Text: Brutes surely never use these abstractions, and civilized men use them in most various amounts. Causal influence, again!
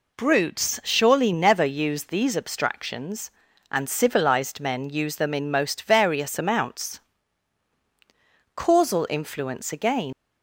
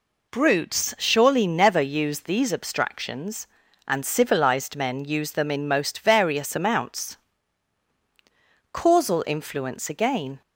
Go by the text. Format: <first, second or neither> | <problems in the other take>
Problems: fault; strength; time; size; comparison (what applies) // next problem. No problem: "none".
second | leaves "again" unfinished; at 10.1 s; 115 ms